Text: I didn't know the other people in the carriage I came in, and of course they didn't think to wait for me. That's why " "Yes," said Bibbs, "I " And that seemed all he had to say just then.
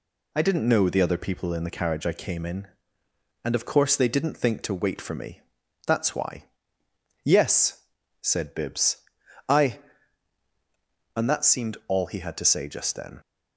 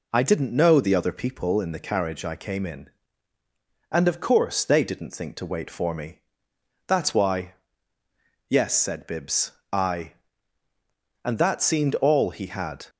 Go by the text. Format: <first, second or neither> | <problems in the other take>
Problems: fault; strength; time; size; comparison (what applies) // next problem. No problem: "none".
first | stops before "to say just then"; at 12.8 s